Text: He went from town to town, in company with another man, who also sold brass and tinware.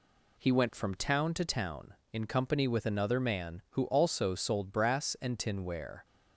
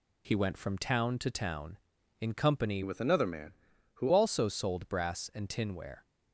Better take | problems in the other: first | changes voice from "with" to "who"; from 2.8 to 4.0 s; 1.2 s long

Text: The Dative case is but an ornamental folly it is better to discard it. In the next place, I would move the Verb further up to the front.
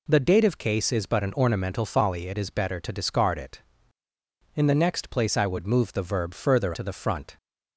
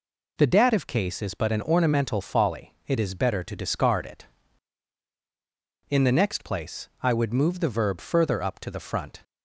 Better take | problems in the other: second | skips "up"; at 6.7 s

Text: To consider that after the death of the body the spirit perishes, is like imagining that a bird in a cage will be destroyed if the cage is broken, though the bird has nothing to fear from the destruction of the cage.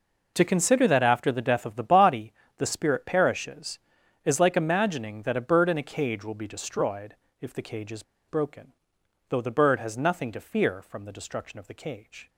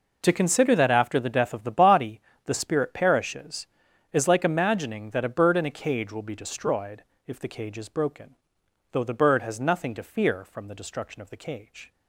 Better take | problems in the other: second | pauses between "body" and "the"; slight; at 2.3 s; 0.24 s long; slight in the second // pauses between "destroyed" and "if"; slight; at 7.1 s; 0.26 s long; slight in the second // pauses between "is" and "broken"; slight; at 8.0 s; 0.26 s long

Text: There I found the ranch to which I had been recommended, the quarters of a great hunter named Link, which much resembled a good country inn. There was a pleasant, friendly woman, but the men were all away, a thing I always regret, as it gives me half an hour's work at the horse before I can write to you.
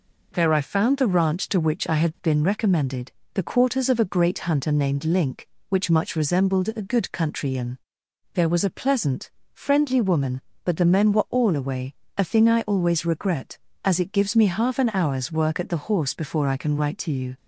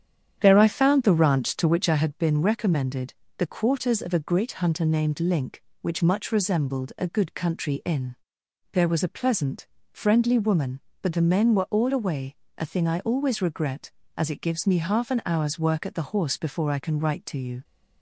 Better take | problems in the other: first | starts louder than the rest; strong; until 1.8 s; 9 dB

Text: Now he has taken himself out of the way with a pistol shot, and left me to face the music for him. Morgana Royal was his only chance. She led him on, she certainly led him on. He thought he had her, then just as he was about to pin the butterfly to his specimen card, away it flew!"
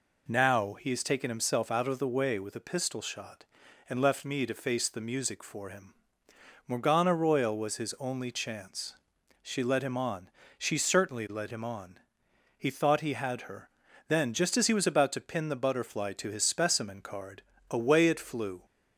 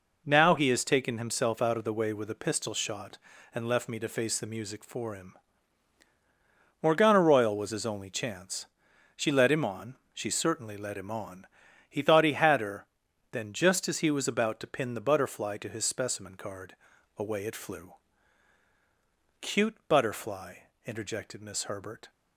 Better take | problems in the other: first | goes on to say "Cute butterfly interjected Miss Herbert"; strong; from 19.4 s on; 2.7 s long

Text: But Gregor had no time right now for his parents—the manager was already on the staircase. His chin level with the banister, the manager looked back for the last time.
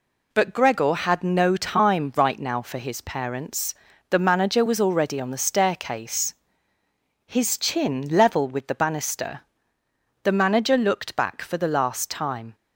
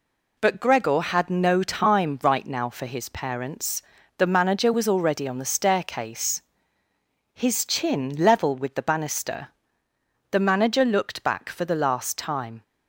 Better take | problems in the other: neither | none

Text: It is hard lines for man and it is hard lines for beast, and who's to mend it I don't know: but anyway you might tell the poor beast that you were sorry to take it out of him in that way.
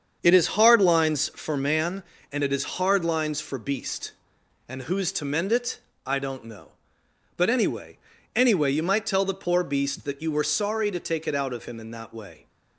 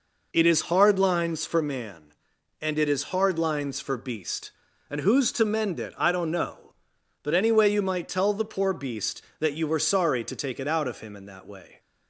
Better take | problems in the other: second | starts louder than the rest; strong; until 1.2 s; 7 dB // pauses between "it" and "I"; slight; at 5.7 s; 0.28 s long // says "anyway" twice; at 8.3 s

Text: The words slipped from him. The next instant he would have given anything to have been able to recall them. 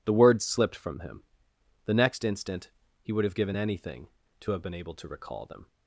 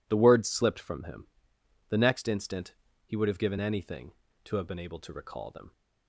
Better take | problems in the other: neither | pauses between "instant" and "he"; slight; the same in both

